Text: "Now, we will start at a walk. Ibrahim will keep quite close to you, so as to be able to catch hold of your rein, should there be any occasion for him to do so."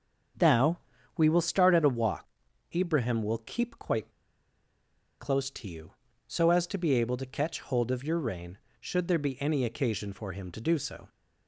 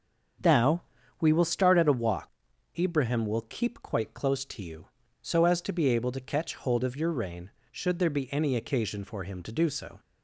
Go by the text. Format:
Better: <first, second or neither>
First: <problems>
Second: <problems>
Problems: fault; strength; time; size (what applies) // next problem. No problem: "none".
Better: second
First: starts louder than the rest; strong; until 1.7 s; 7.5 dB // pauses between "quite" and "close"; at 4.0 s; 1.1 s long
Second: starts louder than the rest; strong; until 1.7 s; 7 dB